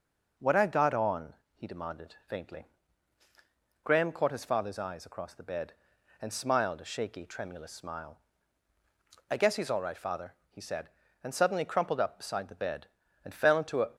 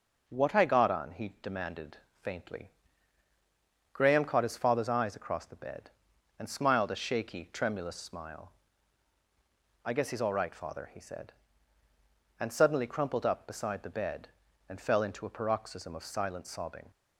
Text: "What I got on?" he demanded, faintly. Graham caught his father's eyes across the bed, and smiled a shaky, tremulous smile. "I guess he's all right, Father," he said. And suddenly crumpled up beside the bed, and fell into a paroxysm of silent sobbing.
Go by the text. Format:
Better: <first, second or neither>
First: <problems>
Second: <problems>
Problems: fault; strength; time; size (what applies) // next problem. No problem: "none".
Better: second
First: stops before "paroxysm of silent sobbing"; at 13.9 s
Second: none